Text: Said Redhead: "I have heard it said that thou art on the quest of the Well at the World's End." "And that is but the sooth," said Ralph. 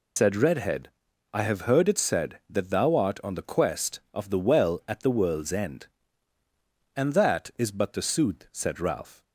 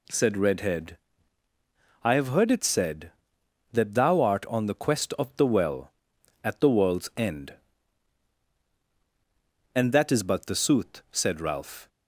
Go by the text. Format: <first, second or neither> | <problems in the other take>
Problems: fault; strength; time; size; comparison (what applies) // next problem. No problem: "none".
second | loses the start of "Said"; at 0.1 s; 95 ms